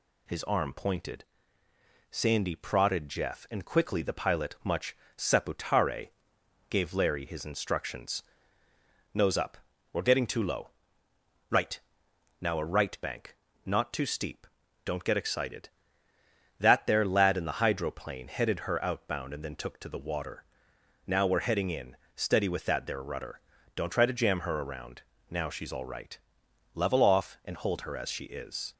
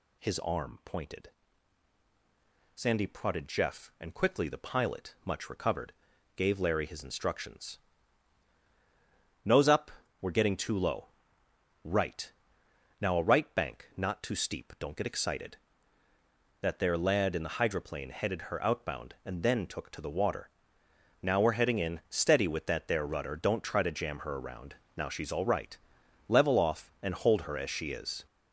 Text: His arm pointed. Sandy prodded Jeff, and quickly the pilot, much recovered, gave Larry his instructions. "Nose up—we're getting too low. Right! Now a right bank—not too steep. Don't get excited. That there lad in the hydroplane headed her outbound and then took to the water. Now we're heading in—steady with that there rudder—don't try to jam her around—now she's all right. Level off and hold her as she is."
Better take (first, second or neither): second